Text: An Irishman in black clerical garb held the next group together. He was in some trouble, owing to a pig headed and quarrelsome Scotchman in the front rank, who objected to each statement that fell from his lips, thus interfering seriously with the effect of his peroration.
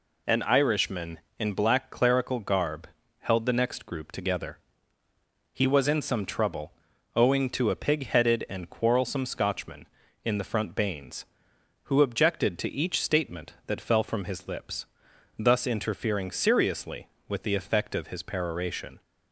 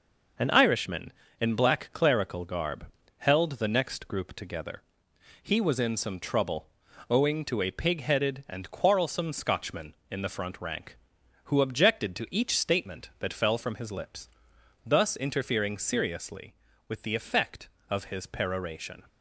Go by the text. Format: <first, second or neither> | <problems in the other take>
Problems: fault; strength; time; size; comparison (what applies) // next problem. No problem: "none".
second | pauses between "garb" and "held"; slight; at 2.8 s; 0.34 s long; slight in the second // says "bains" for "rank"; at 10.7 s